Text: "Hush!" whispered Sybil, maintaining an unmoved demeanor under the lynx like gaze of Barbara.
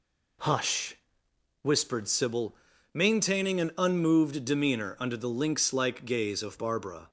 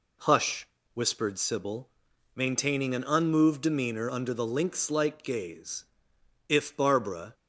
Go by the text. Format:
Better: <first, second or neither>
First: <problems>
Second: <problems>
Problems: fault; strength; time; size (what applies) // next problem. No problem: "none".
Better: first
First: none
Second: says "if" for "of"; at 6.4 s